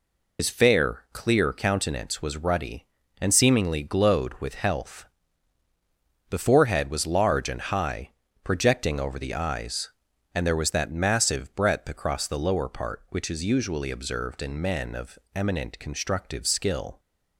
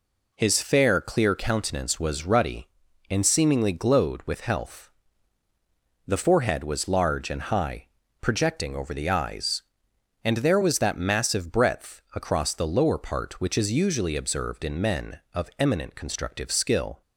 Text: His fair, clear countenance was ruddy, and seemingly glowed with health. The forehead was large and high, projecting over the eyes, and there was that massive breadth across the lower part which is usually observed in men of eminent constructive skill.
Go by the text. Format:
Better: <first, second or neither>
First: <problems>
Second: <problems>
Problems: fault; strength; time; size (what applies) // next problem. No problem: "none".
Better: second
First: loses the start of "His"; at 0.3 s; 95 ms // pauses between "of" and "eminent"; slight; at 15.1 s; 0.16 s long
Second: none